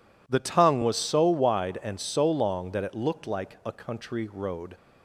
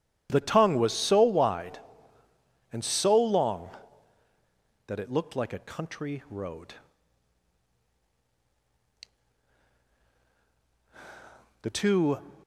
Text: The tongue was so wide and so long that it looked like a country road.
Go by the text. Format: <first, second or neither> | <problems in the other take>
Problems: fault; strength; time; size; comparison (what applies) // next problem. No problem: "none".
first | goes on to say "The two"; from 11.6 s on; 0.57 s long